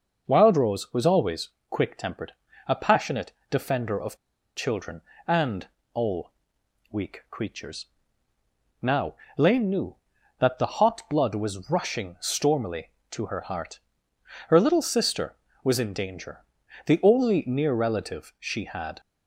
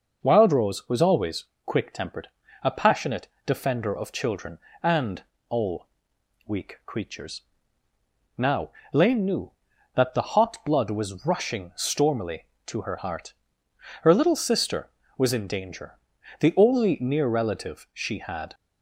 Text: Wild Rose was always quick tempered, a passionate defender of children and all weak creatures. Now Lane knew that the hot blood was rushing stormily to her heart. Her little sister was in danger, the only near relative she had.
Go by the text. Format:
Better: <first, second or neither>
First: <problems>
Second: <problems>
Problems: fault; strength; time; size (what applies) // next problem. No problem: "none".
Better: second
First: pauses between "always" and "quick"; slight; at 1.4 s; 0.22 s long // pauses between "passionate" and "defender"; slight; at 3.3 s; 0.18 s long // pauses between "of" and "children"; at 4.1 s; 0.40 s long // pauses between "and" and "all"; slight; at 5.6 s; 0.26 s long // pauses between "all" and "weak"; noticeable; at 6.3 s; 0.58 s long // pauses between "Now" and "Lane"; slight; at 9.1 s; 0.24 s long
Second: pauses between "always" and "quick"; slight; at 1.4 s; 0.22 s long // pauses between "passionate" and "defender"; slight; at 3.2 s; 0.18 s long // pauses between "and" and "all"; slight; at 5.2 s; 0.26 s long // pauses between "all" and "weak"; noticeable; at 5.8 s; 0.58 s long // pauses between "Now" and "Lane"; slight; at 8.6 s; 0.24 s long